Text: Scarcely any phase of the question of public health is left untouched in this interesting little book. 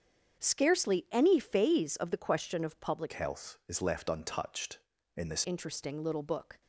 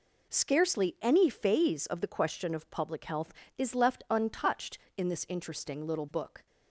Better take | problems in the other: second | starts louder than the rest; strong; until 1.4 s; 7.5 dB // changes voice from "health" to "this"; from 3.1 to 5.4 s; 2.3 s long

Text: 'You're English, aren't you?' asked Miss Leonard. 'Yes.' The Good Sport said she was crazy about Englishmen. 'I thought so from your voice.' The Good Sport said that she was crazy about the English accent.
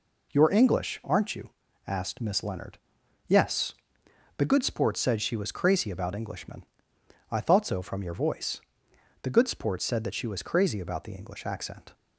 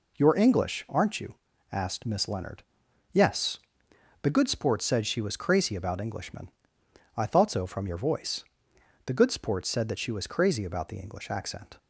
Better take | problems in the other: neither | none

